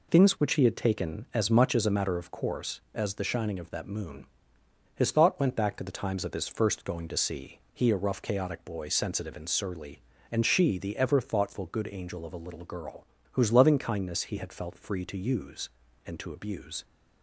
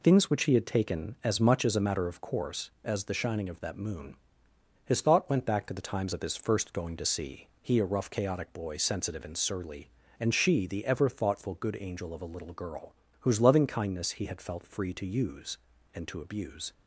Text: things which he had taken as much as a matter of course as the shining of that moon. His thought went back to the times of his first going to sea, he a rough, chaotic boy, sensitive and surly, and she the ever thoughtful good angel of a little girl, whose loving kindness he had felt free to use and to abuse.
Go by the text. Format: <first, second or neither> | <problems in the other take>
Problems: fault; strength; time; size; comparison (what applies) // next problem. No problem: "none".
neither | none